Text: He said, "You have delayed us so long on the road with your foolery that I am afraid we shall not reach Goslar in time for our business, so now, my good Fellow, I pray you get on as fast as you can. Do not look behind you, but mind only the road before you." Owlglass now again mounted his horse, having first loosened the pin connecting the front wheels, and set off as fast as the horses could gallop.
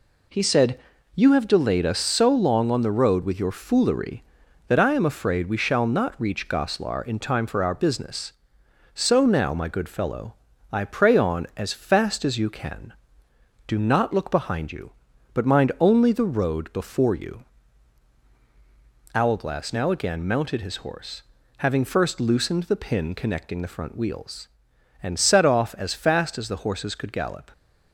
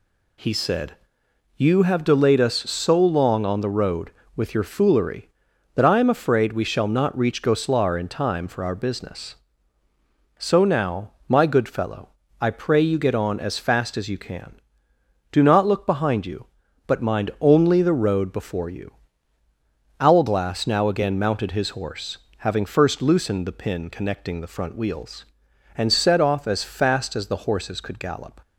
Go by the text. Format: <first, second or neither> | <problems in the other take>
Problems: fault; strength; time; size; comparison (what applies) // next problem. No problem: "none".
second | skips "you get"; at 11.1 s